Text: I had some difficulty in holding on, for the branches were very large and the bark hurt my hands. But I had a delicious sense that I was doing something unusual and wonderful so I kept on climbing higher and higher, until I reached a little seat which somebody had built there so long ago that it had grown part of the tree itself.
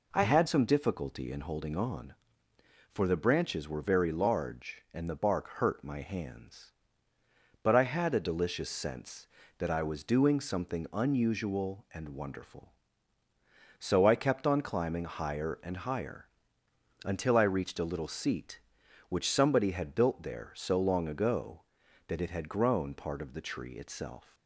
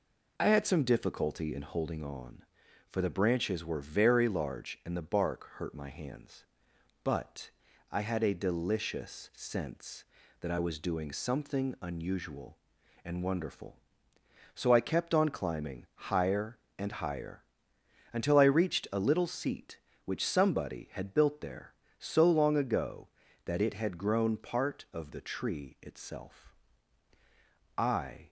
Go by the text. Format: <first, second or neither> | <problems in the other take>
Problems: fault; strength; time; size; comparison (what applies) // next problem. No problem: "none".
first | pauses between "But" and "I"; at 7.4 s; 0.40 s long // goes on to say "I"; from 27.7 s on; 0.52 s long